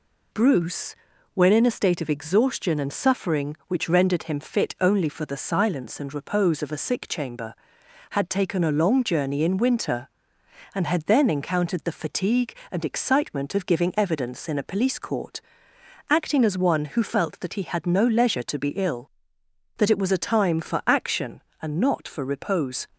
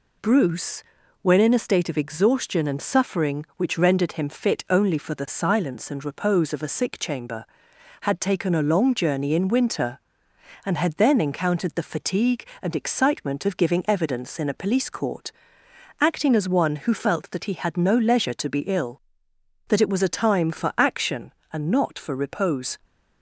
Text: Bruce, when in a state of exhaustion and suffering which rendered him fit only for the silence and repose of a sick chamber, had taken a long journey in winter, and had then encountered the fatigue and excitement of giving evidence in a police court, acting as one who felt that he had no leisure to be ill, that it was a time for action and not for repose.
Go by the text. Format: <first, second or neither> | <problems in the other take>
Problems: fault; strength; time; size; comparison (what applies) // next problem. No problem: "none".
neither | none